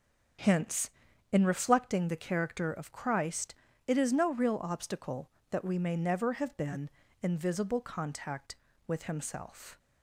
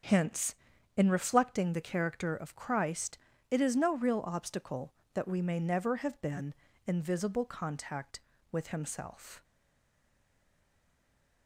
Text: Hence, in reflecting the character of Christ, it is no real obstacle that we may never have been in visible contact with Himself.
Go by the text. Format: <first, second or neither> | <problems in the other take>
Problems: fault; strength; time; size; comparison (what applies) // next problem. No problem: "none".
first | starts louder than the rest; until 1.4 s; 7 dB; also in the first // stays silent after the last word; noticeable; from 9.4 s on; 2.0 s long